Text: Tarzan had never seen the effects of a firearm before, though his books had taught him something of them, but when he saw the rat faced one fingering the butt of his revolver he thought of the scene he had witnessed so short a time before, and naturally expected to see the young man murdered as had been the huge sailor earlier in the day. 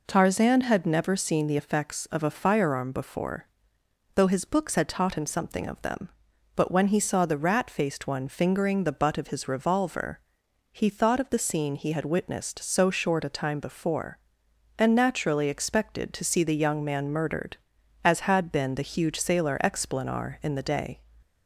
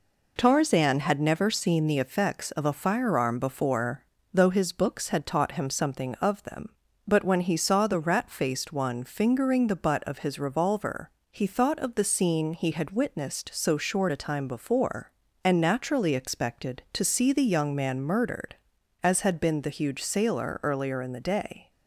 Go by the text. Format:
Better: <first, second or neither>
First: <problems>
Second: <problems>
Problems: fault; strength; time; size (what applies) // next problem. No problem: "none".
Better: second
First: pauses between "revolver" and "he"; noticeable; at 10.1 s; 0.56 s long // says "explanar" for "earlier"; at 19.6 s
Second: pauses between "revolver" and "he"; slight; at 11.0 s; 0.22 s long